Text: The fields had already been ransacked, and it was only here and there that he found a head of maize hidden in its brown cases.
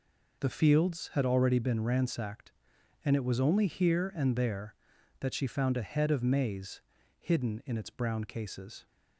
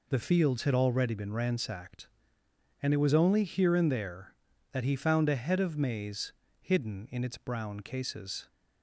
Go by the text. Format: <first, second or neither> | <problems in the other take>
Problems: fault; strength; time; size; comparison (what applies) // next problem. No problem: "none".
second | says "she" for "he"; at 5.3 s // pauses between "maize" and "hidden"; at 6.8 s; 0.38 s long; slight in the second